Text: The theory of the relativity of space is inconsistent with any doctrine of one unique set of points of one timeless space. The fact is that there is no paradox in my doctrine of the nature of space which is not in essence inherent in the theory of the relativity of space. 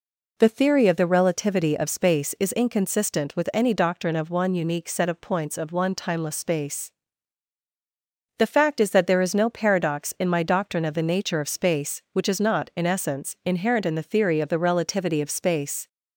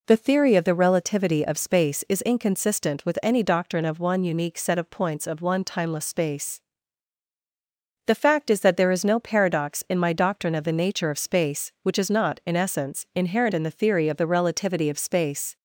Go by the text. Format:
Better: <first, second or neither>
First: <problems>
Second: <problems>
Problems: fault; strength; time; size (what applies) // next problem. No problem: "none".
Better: neither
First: none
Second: none